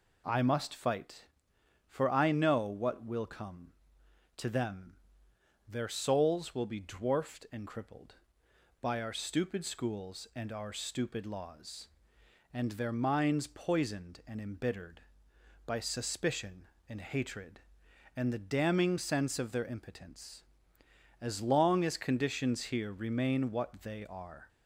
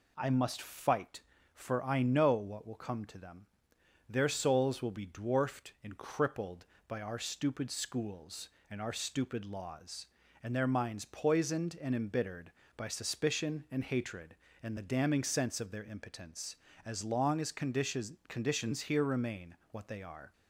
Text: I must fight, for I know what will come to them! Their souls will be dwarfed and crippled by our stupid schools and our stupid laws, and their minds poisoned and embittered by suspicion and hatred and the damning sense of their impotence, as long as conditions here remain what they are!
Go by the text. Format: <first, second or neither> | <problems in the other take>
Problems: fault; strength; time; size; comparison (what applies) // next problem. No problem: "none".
first | says "conditions" twice; at 18.2 s